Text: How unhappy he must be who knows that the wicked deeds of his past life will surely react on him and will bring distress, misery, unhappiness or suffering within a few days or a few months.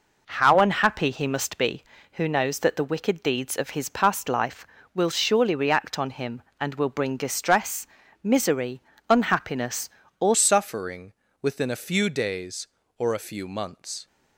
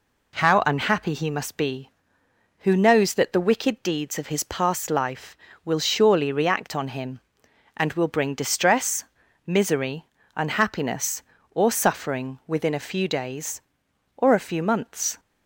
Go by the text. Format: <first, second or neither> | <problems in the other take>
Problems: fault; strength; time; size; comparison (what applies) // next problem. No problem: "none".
second | changes voice at "suffering"; from 10.3 s on; 3.7 s long // pauses between "suffering" and "within"; slight; at 11.1 s; 0.28 s long